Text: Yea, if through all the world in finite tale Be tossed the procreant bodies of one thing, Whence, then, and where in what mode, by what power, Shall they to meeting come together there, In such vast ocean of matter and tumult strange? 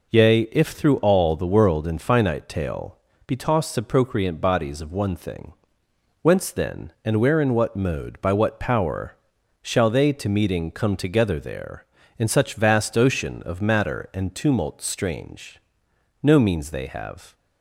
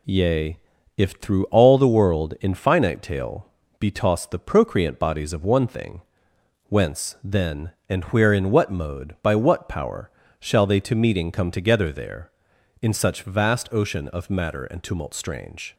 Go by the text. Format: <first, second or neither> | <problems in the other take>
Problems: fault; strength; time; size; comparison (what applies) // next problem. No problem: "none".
second | pauses between "tale" and "Be"; slight; at 2.9 s; 0.30 s long; slight in the second // goes on to say "No means they have"; noticeable; from 16.2 s on; 1.1 s long